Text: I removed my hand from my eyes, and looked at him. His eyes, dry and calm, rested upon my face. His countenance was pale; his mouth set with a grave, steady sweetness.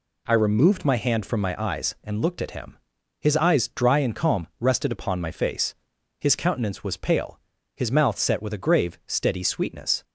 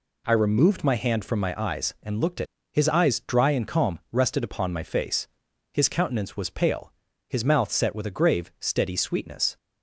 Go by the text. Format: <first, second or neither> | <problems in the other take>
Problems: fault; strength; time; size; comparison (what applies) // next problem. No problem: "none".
first | skips "him"; at 2.5 s